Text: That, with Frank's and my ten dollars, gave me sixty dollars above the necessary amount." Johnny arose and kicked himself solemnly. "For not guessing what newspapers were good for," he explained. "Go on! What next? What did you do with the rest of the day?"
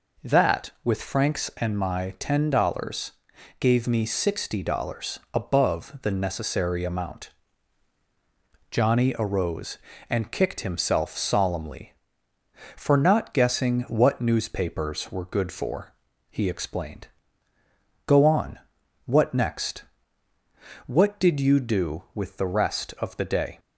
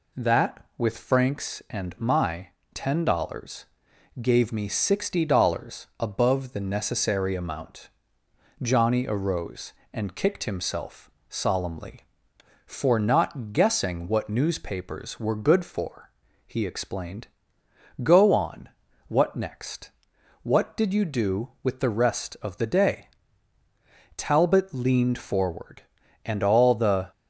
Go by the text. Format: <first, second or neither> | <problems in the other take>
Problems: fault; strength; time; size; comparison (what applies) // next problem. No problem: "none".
first | pauses between "my" and "ten"; slight; at 2.4 s; 0.26 s long // pauses between "himself" and "solemnly"; slight; at 11.1 s; 0.18 s long // goes on to say "Talbot leaned forward and all the"; strong; from 24.1 s on; 2.9 s long